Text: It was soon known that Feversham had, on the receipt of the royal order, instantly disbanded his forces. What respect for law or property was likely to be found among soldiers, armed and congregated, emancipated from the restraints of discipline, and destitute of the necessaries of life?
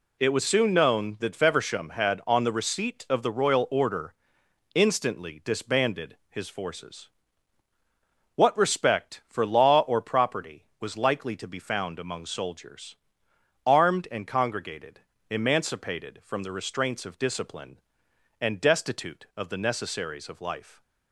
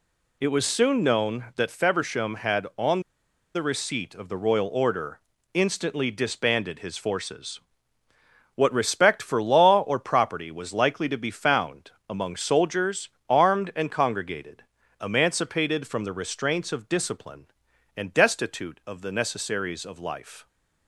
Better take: first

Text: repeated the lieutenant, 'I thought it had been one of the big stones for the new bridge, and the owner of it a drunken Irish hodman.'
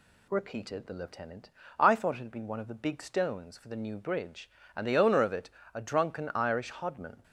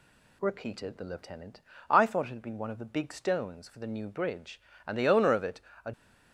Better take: first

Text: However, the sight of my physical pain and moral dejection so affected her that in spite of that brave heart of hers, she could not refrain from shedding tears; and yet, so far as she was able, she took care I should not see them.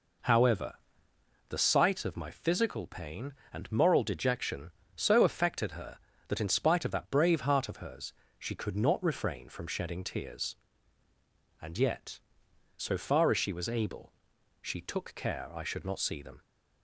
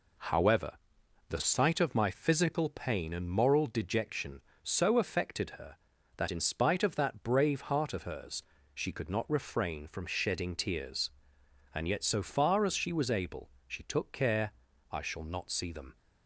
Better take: first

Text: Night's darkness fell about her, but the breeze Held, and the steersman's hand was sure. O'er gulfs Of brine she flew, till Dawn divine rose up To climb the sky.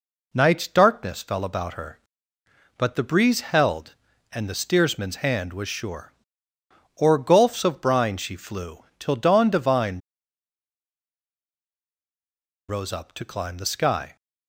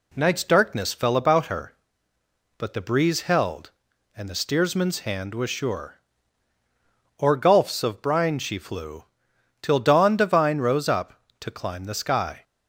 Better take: second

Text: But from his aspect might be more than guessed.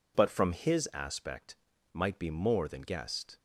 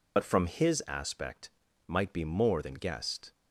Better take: first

